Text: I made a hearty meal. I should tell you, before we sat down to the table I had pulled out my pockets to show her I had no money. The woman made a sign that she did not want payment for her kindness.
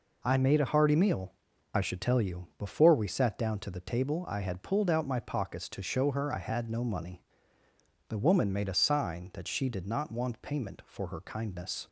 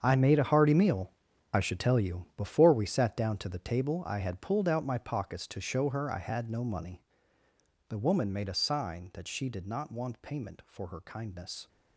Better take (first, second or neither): first